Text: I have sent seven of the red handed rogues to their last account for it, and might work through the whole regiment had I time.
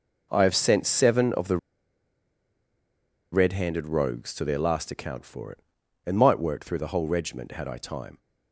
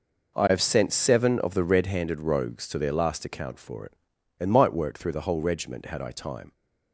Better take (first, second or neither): second